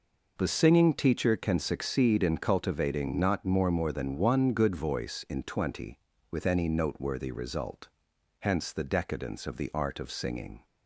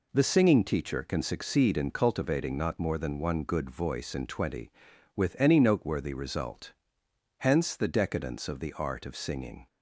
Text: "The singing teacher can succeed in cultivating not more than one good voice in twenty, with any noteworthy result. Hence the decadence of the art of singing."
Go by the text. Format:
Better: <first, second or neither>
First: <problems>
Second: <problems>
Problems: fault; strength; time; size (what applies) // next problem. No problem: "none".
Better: second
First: says "more" twice; at 3.7 s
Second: none